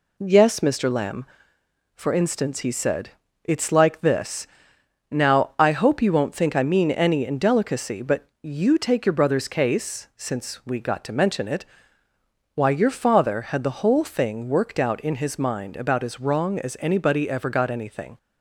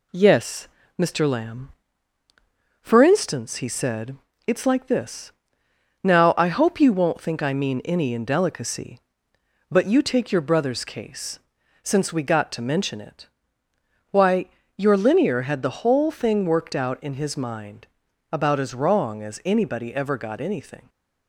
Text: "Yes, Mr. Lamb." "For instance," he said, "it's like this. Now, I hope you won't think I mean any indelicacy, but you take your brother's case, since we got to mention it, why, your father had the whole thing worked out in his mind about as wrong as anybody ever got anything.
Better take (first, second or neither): first